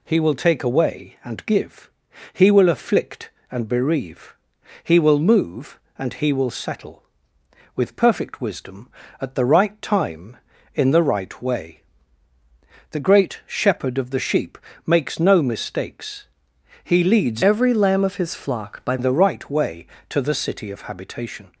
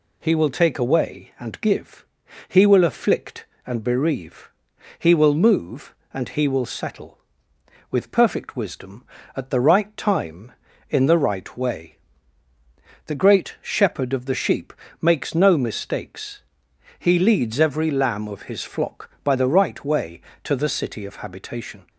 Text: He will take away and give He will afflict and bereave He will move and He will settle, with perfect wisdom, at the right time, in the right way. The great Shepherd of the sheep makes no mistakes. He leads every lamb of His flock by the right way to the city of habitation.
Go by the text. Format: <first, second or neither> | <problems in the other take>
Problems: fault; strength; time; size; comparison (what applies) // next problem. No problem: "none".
second | pauses between "give" and "He"; at 1.9 s; 0.42 s long; also in the second // pauses between "bereave" and "He"; noticeable; at 4.3 s; 0.48 s long; noticeable in the second // pauses between "sheep" and "makes"; slight; at 14.5 s; 0.28 s long; slight in the second // changes voice from "every" to "by"; from 17.4 to 18.9 s; 1.5 s long